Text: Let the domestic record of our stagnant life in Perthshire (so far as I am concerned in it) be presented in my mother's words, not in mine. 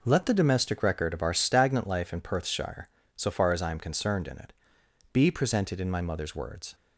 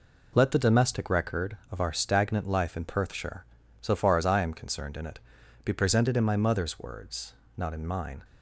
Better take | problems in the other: second | stops before "not in mine"; at 6.7 s

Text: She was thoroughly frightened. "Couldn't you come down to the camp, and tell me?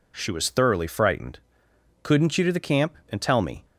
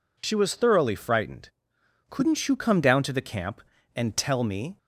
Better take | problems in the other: second | skips "come down"; at 2.4 s

